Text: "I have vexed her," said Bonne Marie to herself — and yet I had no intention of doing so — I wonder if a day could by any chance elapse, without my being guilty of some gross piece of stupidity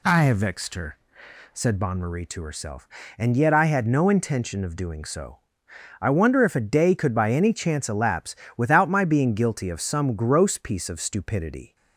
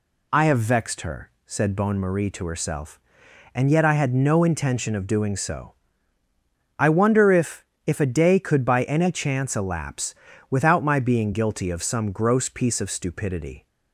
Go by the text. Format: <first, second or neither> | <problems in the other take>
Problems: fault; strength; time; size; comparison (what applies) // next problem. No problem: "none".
first | says "if" twice; at 7.8 s